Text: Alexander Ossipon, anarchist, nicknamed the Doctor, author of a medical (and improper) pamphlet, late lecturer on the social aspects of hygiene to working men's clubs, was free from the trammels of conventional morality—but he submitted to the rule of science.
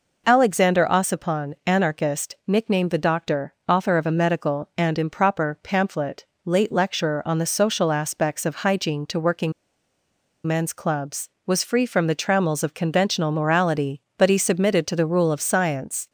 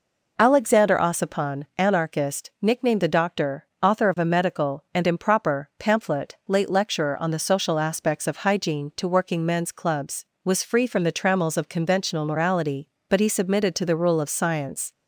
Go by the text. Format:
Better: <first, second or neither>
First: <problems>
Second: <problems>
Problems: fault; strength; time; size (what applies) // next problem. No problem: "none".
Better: second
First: pauses between "working" and "men's"; noticeable; at 9.5 s; 0.93 s long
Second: none